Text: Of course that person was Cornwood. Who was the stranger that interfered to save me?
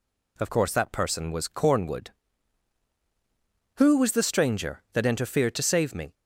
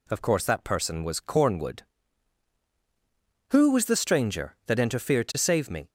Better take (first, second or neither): neither